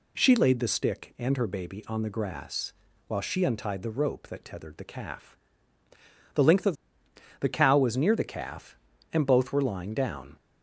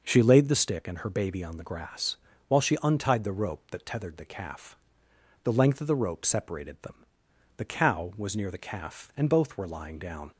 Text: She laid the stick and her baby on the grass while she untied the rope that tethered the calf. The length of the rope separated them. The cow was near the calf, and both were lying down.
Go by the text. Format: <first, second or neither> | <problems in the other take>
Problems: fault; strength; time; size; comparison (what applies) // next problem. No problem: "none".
second | pauses between "grass" and "while"; slight; at 2.7 s; 0.34 s long; slight in the second // skips "the rope separated them"; at 7.0 s